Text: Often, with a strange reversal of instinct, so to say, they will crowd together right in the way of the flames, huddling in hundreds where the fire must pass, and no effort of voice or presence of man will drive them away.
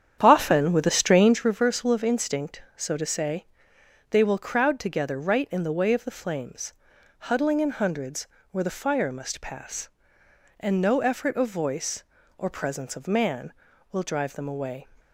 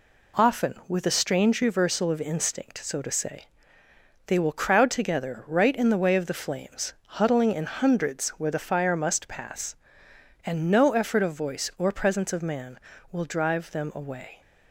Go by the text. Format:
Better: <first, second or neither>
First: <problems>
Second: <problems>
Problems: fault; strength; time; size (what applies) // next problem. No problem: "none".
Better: second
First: starts louder than the rest; strong; until 1.5 s; 9 dB // pauses between "hundreds" and "where"; slight; at 8.2 s; 0.24 s long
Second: none